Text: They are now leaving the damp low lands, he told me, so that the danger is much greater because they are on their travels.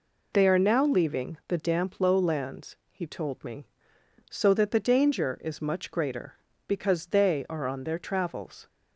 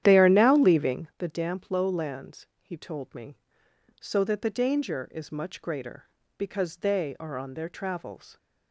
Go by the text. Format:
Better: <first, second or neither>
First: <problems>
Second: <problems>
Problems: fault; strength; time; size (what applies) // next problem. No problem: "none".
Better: first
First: none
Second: starts louder than the rest; strong; until 1.1 s; 10.5 dB